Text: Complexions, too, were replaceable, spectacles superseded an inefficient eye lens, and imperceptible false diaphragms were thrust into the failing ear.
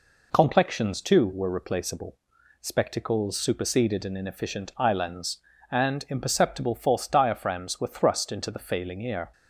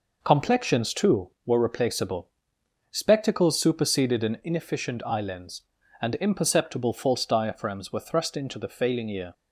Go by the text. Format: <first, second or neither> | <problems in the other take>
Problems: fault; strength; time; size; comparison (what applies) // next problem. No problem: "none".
neither | none